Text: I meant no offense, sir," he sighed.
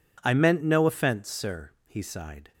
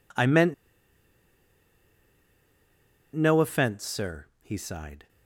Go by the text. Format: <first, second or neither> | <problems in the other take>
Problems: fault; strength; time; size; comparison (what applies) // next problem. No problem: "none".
first | pauses between "meant" and "no"; strong; at 0.5 s; 2.6 s long